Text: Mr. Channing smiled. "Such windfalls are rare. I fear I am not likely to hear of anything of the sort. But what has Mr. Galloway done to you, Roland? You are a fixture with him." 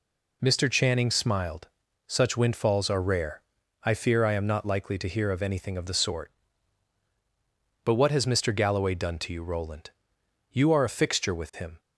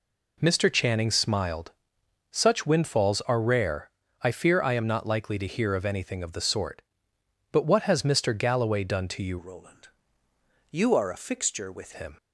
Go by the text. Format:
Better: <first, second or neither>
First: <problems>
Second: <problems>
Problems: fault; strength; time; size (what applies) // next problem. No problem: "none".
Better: first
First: none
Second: changes voice from "Roland" to "with"; from 9.3 to 11.9 s; 2.6 s long